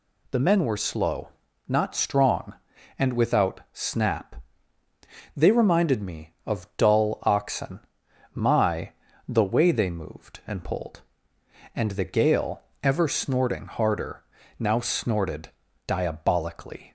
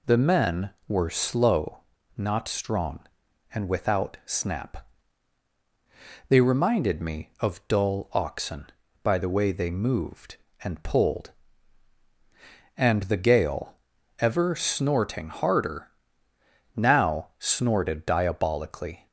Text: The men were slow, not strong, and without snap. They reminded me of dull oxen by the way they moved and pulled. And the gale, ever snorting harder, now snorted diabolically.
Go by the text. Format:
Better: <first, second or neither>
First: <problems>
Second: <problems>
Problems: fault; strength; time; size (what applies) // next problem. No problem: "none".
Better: second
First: says "my" for "by"; at 8.3 s // pauses between "snorted" and "diabolically"; slight; at 15.5 s; 0.36 s long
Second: none